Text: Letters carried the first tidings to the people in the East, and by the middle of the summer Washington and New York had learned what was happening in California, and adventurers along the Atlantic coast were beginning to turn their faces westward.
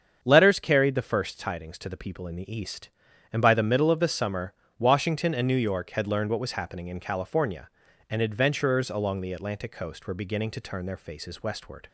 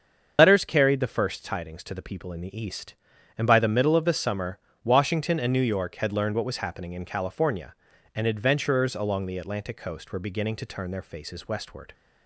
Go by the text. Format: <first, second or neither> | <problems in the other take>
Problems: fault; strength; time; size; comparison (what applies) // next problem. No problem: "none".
first | loses the start of "Letters"; at 0.3 s; 105 ms // starts louder than the rest; until 1.3 s; 7 dB; strong in the first // pauses between "summer" and "Washington"; slight; at 4.5 s; 0.26 s long; slight in the first